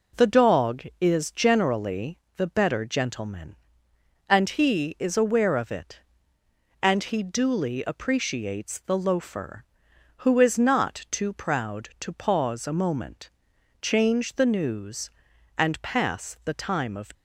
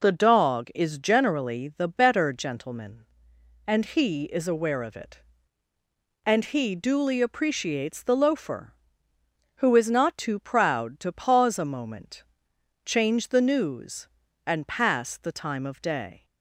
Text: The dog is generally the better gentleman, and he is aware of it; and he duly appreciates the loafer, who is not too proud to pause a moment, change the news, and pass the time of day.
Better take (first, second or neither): second